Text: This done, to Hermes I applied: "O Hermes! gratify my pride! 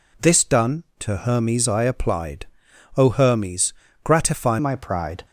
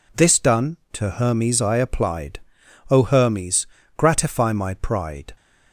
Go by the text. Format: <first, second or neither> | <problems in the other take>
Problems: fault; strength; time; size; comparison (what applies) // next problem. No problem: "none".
second | changes voice at "my"; from 4.5 s on; 0.7 s long